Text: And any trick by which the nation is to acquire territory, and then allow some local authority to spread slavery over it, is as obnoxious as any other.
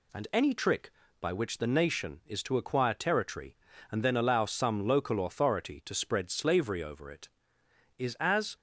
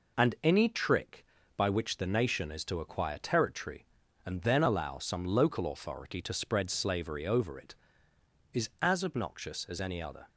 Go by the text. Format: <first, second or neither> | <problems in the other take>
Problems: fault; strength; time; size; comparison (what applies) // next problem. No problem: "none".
second | stops before "obnoxious as any other"; at 8.5 s